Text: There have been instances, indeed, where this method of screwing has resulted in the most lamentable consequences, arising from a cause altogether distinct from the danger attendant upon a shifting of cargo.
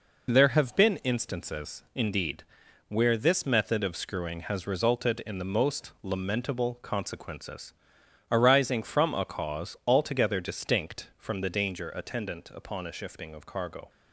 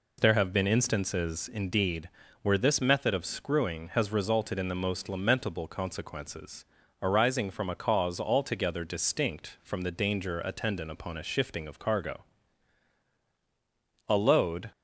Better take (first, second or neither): first